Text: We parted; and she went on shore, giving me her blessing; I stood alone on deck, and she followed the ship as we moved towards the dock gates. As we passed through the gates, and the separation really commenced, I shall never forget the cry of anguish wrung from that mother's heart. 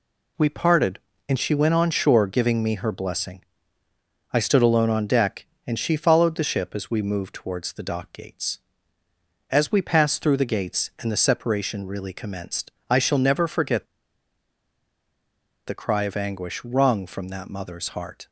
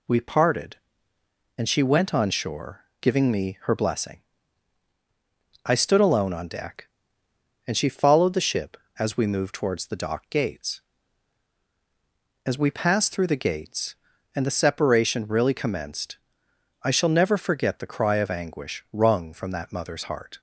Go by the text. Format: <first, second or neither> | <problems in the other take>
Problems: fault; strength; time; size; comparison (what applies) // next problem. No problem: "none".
second | pauses between "forget" and "the"; strong; at 13.8 s; 1.7 s long